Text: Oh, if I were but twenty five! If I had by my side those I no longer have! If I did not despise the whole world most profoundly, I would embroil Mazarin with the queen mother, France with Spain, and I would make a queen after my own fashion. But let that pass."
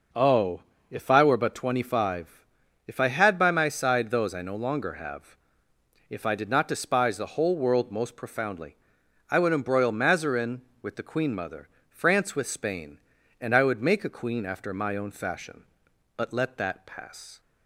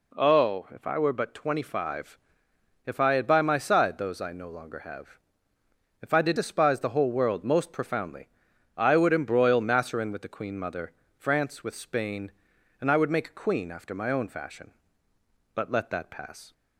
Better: first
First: none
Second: skips "not"; at 6.3 s

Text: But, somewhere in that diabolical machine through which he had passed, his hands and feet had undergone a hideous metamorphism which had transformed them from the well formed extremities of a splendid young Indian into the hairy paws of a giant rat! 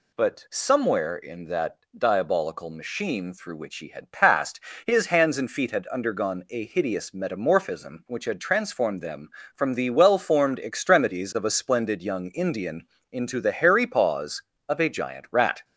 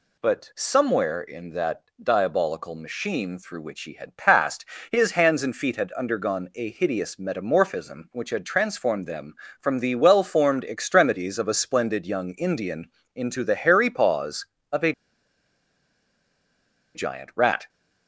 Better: first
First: pauses between "that" and "diabolical"; slight; at 1.7 s; 0.18 s long // pauses between "Indian" and "into"; slight; at 12.8 s; 0.24 s long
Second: pauses between "that" and "diabolical"; slight; at 1.8 s; 0.18 s long // pauses between "Indian" and "into"; slight; at 12.8 s; 0.24 s long // pauses between "a" and "giant"; strong; at 14.9 s; 2.0 s long

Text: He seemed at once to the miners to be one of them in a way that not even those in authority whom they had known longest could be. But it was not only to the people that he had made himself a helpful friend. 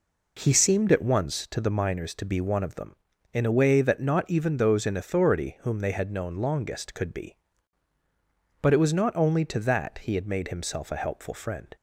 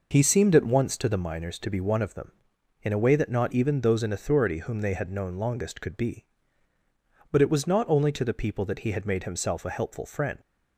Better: second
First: skips "the people"; at 9.5 s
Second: none

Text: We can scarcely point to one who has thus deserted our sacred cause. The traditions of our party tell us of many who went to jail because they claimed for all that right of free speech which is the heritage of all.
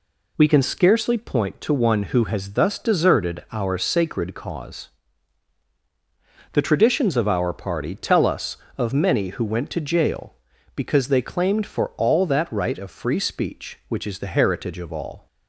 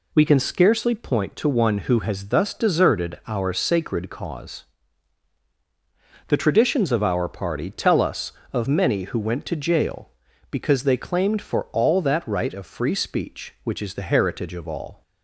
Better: neither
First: none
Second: none

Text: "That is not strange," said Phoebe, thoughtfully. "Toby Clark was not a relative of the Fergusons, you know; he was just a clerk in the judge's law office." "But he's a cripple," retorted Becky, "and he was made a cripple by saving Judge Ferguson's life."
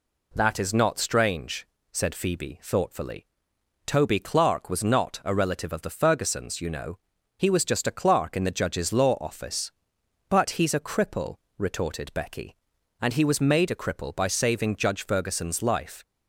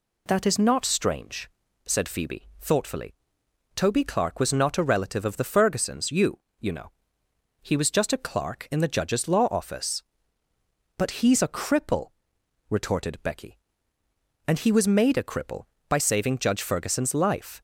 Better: first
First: none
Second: says "you" twice; at 6.5 s

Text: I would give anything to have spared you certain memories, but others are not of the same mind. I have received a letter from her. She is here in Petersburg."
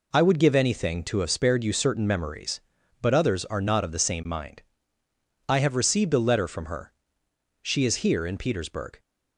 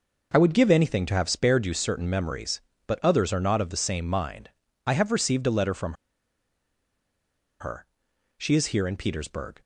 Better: first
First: none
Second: pauses between "from" and "her"; strong; at 5.9 s; 1.6 s long

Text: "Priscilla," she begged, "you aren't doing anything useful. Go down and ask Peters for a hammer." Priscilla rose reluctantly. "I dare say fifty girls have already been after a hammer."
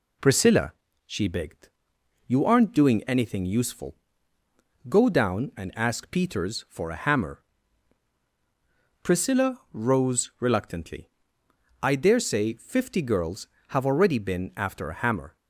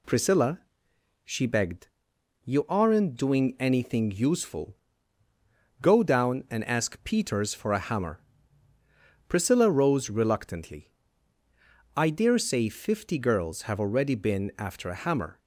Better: neither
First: none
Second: none

